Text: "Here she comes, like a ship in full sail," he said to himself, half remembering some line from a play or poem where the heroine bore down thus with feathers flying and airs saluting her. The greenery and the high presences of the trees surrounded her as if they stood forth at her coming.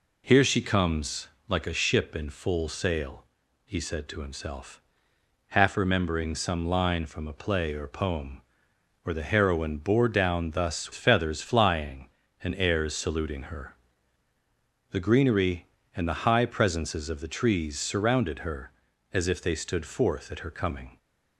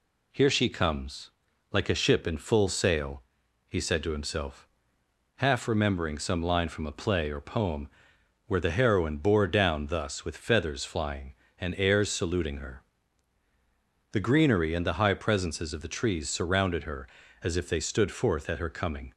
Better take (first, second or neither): second